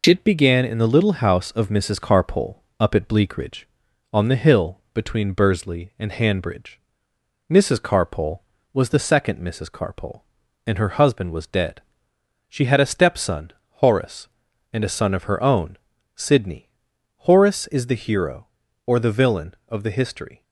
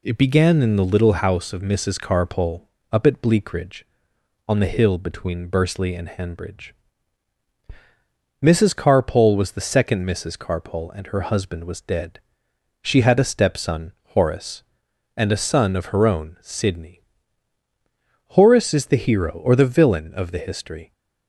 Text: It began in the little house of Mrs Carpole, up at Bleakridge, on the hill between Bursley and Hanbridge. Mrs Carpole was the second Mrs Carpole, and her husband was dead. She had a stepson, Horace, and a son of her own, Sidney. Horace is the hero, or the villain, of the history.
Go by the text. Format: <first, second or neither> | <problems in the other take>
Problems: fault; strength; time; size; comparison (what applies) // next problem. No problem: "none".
neither | none